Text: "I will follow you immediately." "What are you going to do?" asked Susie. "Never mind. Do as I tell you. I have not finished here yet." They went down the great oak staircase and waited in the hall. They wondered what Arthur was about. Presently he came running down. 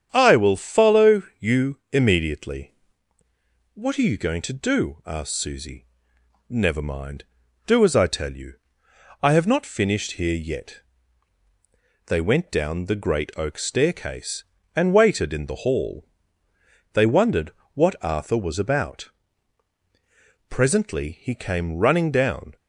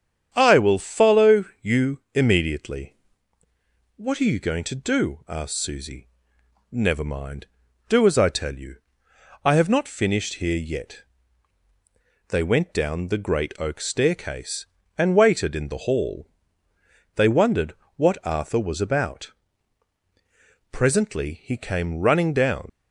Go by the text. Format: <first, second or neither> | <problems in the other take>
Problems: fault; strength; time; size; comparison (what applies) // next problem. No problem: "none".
first | starts louder than the rest; strong; until 1.3 s; 8.5 dB; strong in the first // pauses between "follow" and "you"; slight; at 1.4 s; 0.18 s long; slight in the first // pauses between "wondered" and "what"; slight; at 17.7 s; 0.24 s long; slight in the first // leaves "down" unfinished; at 22.6 s; 80 ms